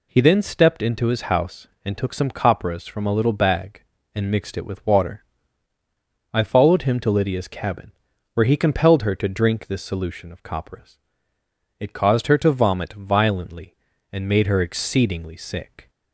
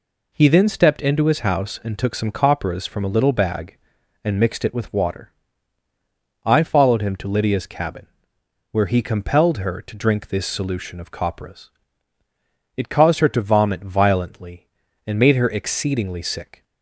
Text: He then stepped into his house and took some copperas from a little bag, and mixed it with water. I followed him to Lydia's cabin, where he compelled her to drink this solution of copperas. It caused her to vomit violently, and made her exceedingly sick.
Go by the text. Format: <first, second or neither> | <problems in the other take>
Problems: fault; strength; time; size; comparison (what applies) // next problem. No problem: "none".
neither | none